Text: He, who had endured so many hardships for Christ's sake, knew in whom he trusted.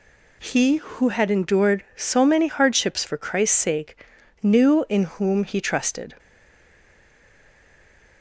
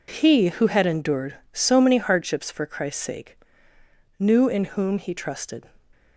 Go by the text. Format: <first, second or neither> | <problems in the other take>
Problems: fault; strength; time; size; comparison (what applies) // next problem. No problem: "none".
second | stays silent after the last word; noticeable; from 6.1 s on; 2.1 s long